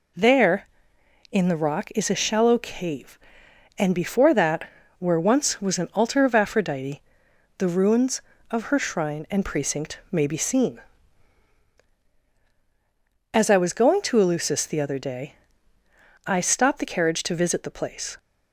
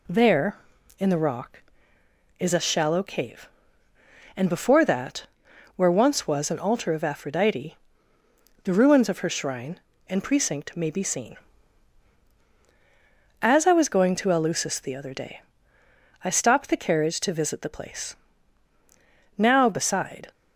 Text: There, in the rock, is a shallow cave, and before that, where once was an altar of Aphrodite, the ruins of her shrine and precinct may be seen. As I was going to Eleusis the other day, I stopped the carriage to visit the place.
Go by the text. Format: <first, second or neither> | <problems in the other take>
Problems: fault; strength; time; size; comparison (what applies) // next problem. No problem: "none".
first | goes on to say "Now beside"; noticeable; from 19.3 s on; 0.94 s long